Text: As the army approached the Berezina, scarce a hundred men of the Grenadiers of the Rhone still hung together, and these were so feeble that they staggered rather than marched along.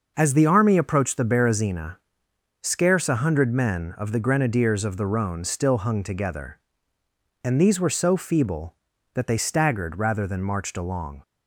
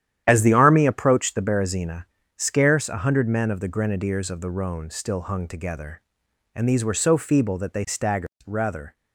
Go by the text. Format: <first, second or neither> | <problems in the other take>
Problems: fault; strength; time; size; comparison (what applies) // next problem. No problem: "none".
first | starts louder than the rest; strong; until 1.2 s; 10.5 dB; noticeable in the first // pauses between "staggered" and "rather"; slight; at 8.2 s; 0.16 s long // stops before "than marched along"; at 8.9 s